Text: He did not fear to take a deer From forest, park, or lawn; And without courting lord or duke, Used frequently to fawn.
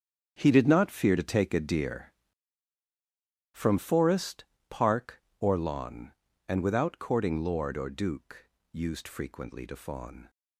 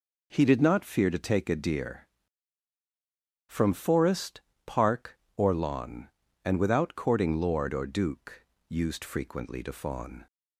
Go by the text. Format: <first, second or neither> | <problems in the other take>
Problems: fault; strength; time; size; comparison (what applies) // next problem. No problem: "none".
second | gets quieter; strong; throughout; 12.5 dB